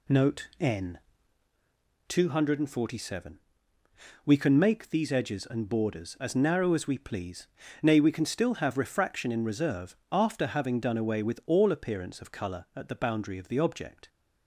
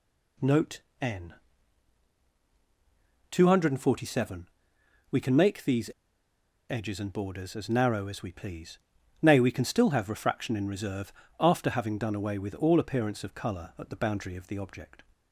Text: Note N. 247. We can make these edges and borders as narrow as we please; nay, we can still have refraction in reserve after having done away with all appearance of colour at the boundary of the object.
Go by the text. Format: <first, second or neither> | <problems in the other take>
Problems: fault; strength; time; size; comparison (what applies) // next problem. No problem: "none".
first | pauses between "Note" and "N"; slight; at 0.8 s; 0.20 s long // pauses between "these" and "edges"; noticeable; at 5.8 s; 0.82 s long // pauses between "reserve" and "after"; slight; at 11.1 s; 0.26 s long; slight in the first